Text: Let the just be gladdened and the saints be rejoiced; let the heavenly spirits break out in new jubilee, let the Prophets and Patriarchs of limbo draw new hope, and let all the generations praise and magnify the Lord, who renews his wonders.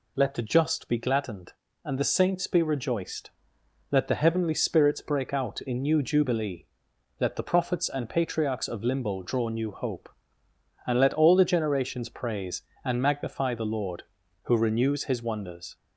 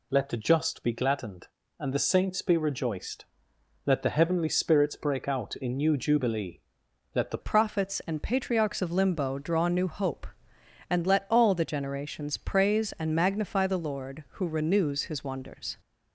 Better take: first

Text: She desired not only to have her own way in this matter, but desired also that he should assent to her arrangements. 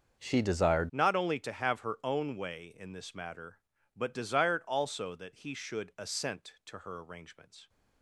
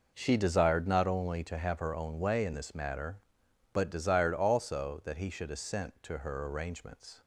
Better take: second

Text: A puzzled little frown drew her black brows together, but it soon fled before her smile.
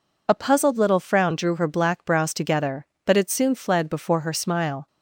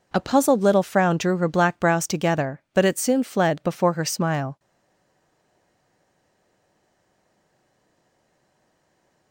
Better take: first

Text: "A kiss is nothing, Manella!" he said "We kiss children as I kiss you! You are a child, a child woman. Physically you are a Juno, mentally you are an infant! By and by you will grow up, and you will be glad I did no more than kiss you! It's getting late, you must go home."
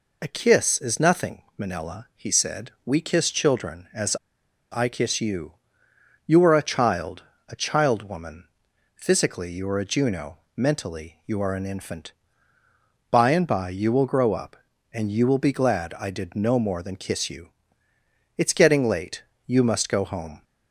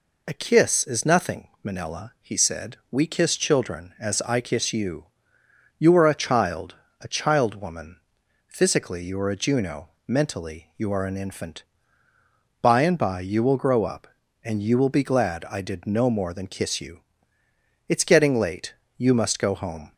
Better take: second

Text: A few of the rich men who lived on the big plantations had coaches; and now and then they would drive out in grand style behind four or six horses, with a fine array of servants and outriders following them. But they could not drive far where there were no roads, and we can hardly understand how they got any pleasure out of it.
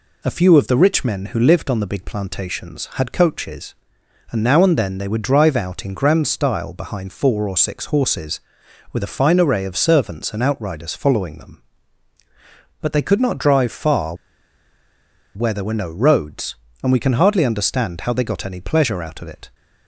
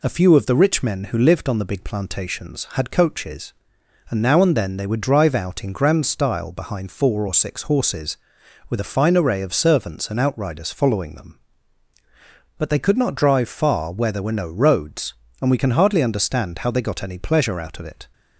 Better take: second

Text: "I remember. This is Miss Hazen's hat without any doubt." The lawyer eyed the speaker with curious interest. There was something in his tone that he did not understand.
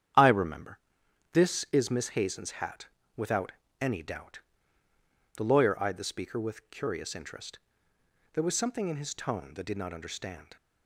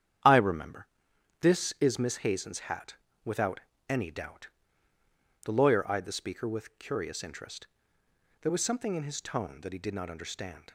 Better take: second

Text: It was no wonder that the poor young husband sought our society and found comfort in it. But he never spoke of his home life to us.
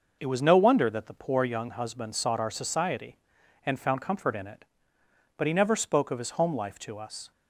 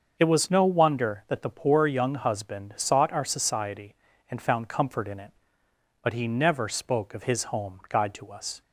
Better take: first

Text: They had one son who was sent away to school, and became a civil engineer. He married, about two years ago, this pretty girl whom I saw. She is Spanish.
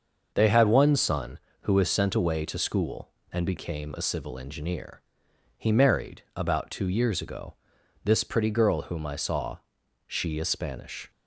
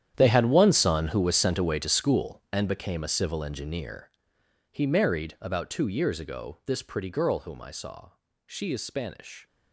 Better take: first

